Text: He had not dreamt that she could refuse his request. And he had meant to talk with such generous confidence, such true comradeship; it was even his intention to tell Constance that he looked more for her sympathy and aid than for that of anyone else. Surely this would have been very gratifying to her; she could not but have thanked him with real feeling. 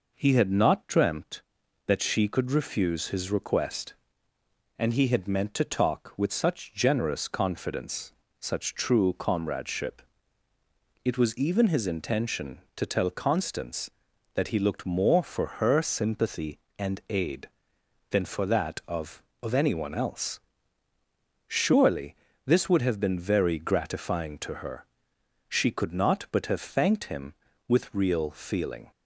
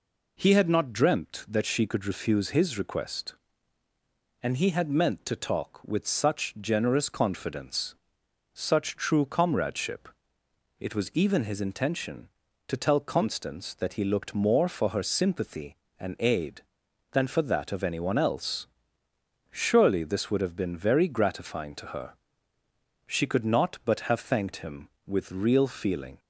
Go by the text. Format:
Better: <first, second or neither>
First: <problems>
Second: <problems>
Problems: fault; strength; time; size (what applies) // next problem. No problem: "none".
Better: second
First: says "of" twice; at 19.4 s // pauses between "Surely" and "this"; slight; at 22.1 s; 0.30 s long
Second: none